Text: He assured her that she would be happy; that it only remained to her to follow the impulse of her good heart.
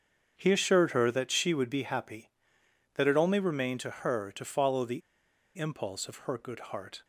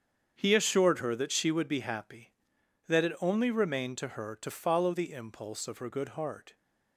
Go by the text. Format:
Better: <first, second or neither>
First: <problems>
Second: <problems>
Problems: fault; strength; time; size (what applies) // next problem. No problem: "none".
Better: second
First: starts louder than the rest; strong; until 1.4 s; 7 dB // pauses between "the" and "impulse"; noticeable; at 5.0 s; 0.57 s long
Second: starts louder than the rest; strong; until 1.3 s; 7.5 dB